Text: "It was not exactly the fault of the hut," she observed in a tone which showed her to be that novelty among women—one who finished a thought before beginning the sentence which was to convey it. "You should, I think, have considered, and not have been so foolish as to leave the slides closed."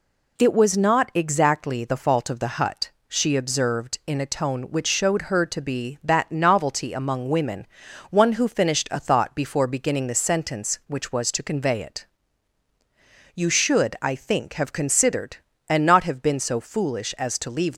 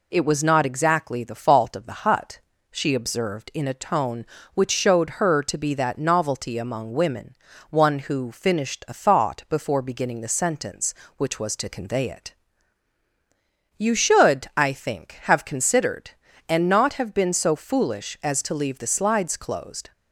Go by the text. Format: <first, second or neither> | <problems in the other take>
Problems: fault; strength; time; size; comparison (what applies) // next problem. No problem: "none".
second | stops before "the slides closed"; at 17.7 s